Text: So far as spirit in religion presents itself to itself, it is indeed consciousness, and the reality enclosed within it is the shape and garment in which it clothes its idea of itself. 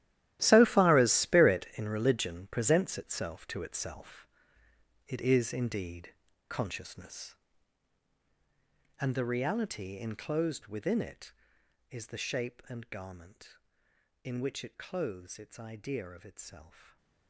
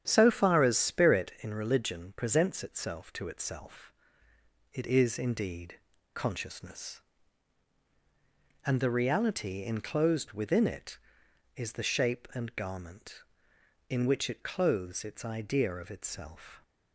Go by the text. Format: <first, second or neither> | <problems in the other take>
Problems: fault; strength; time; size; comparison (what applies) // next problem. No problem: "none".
second | gets quieter; strong; throughout; 16.5 dB // starts louder than the rest; strong; until 1.4 s; 14 dB; strong in the second // pauses between "indeed" and "consciousness"; slight; at 6.1 s; 0.34 s long; slight in the second // stays silent after the last word; slight; from 16.6 s on; 0.6 s long